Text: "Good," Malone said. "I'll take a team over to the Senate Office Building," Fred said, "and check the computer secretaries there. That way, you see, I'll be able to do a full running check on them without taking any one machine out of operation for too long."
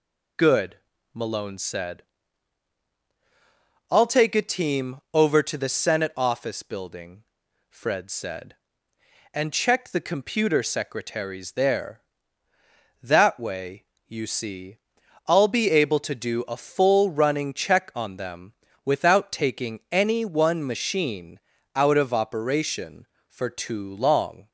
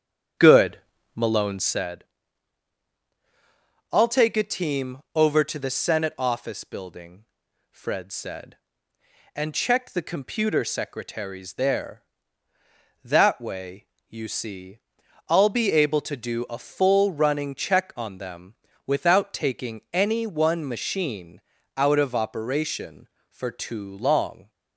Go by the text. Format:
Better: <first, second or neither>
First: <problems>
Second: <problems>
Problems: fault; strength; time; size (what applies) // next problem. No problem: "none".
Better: first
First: pauses between "them" and "without"; slight; at 18.5 s; 0.30 s long // pauses between "machine" and "out"; slight; at 21.3 s; 0.34 s long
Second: starts louder than the rest; strong; until 1.9 s; 8.5 dB // pauses between "them" and "without"; slight; at 18.5 s; 0.30 s long // pauses between "machine" and "out"; slight; at 21.4 s; 0.34 s long